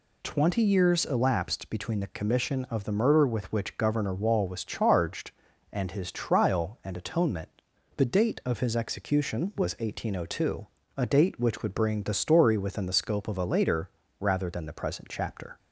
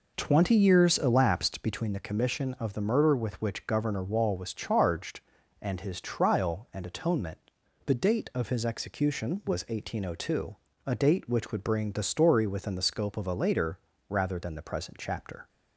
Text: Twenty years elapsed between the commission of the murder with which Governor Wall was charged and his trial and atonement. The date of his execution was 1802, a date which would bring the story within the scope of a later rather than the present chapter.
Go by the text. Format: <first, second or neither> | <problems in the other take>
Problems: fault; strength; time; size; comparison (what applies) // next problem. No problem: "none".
first | starts louder than the rest; noticeable; until 1.9 s; 5 dB // pauses between "later" and "rather"; slight; at 13.7 s; 0.28 s long; slight in the first